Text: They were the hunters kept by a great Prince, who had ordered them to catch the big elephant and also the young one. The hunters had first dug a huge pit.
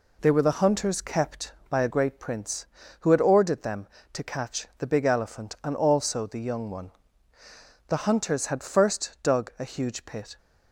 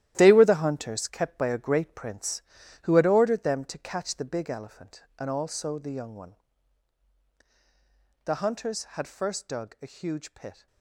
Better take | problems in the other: first | gets quieter; strong; throughout; 11.5 dB

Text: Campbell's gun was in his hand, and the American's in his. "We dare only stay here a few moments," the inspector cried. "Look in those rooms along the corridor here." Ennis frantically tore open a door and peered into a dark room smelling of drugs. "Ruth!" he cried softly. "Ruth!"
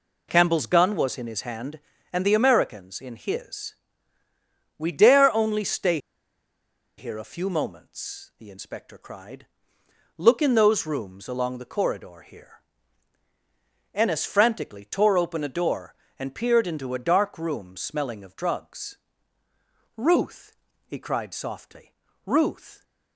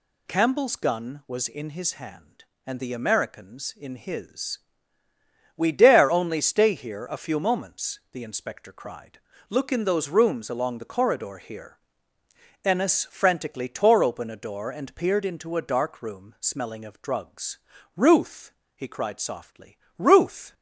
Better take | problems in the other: second | pauses between "stay" and "here"; at 5.9 s; 1.0 s long

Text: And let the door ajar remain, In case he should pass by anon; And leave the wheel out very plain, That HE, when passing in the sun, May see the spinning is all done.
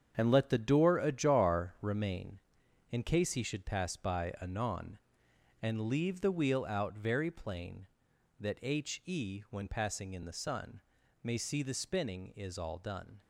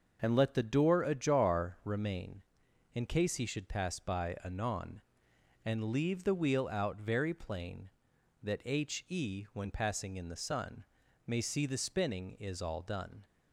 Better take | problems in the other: second | gets quieter; strong; throughout; 10 dB // starts louder than the rest; strong; until 1.1 s; 7.5 dB; noticeable in the second

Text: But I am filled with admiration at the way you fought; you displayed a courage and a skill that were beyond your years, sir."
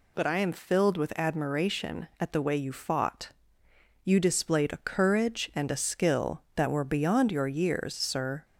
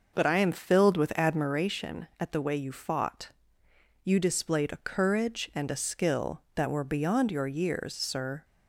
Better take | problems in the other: first | starts louder than the rest; noticeable; until 1.7 s; 6 dB

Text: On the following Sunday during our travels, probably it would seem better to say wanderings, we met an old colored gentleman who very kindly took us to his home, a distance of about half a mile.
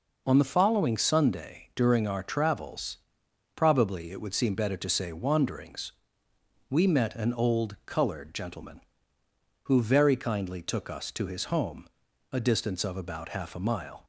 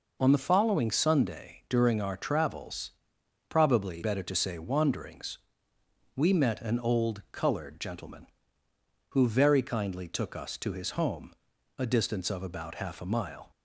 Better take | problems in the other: first | skips "it would seem"; at 4.0 s

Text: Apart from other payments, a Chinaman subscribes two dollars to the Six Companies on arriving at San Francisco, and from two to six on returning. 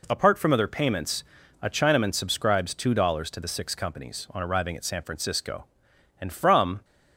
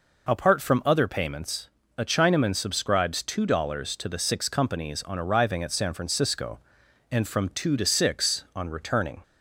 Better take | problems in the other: second | stops before "two to six on returning"; at 6.8 s

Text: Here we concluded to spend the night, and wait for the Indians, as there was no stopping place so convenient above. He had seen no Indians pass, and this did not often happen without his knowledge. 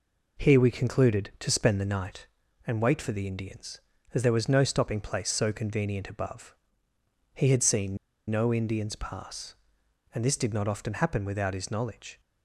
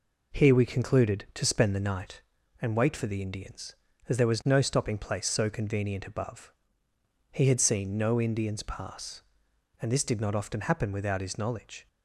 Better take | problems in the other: second | pauses between "seen" and "no"; slight; at 7.9 s; 0.32 s long

